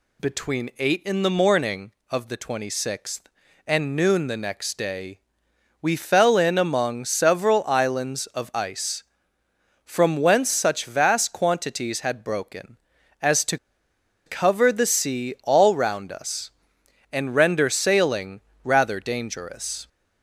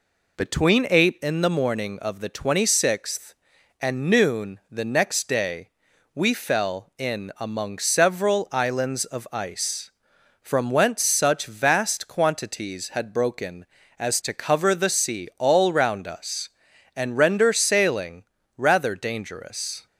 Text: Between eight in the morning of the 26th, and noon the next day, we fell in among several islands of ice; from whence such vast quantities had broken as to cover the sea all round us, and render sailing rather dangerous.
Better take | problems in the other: second | pauses between "to" and "cover"; noticeable; at 13.5 s; 0.69 s long // pauses between "sailing" and "rather"; slight; at 18.3 s; 0.24 s long; slight in the second

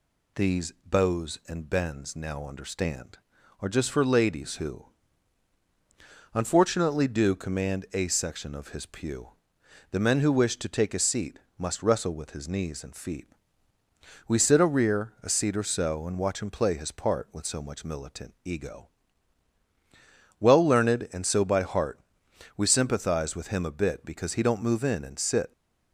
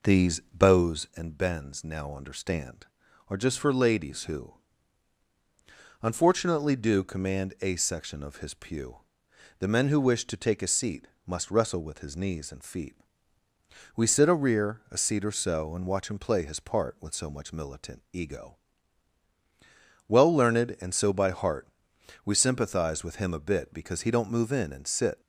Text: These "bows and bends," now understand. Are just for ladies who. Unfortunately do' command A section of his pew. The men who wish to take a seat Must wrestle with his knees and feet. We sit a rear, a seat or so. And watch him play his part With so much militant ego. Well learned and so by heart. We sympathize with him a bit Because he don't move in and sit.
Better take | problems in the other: first | starts louder than the rest; noticeable; until 1.2 s; 4.5 dB // pauses between "seat" and "Must"; slight; at 11.0 s; 0.20 s long; slight in the first

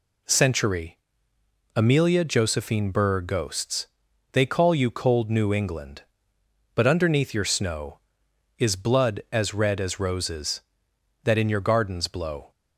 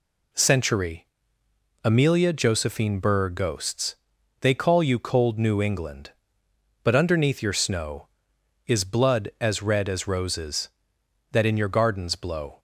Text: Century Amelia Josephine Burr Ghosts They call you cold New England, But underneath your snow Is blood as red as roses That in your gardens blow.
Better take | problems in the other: neither | pauses between "Century" and "Amelia"; noticeable; the same in both // pauses between "Ghosts" and "They"; the same in both

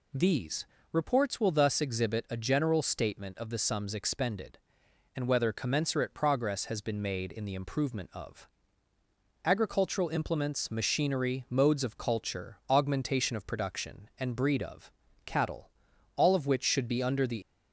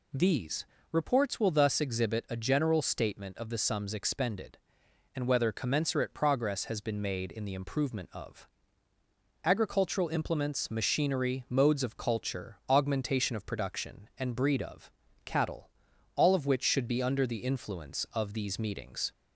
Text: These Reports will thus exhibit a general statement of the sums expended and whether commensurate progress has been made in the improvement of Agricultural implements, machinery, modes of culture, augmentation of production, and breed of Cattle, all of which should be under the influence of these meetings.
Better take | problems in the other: second | pauses between "These" and "Reports"; slight; at 0.6 s; 0.28 s long; slight in the second // pauses between "of" and "Agricultural"; noticeable; at 8.4 s; 0.96 s long; noticeable in the second // pauses between "of" and "Cattle"; slight; at 14.8 s; 0.36 s long; slight in the second // stops before "influence of these meetings"; at 17.4 s

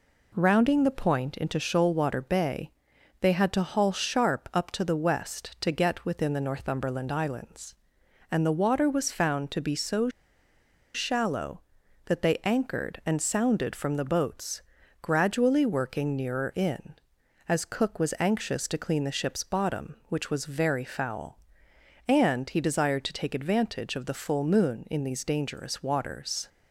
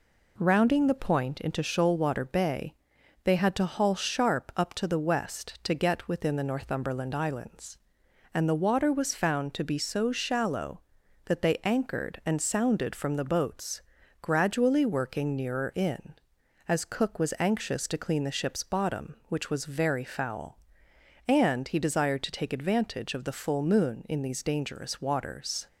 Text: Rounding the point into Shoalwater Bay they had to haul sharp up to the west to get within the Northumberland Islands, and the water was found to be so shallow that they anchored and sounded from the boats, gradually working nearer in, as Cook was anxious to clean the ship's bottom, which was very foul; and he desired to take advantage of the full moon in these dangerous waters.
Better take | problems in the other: second | pauses between "Bay" and "they"; noticeable; at 2.7 s; 0.50 s long; noticeable in the second // pauses between "so" and "shallow"; noticeable; at 10.0 s; 0.85 s long

